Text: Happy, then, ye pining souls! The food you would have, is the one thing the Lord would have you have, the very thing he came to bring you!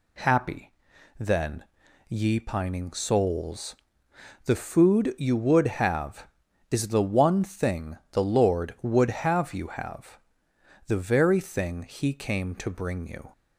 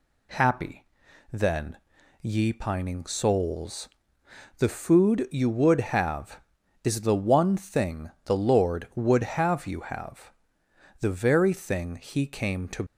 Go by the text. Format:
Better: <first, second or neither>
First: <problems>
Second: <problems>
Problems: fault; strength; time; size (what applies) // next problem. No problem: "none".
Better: first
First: none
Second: stops before "bring you"; at 12.8 s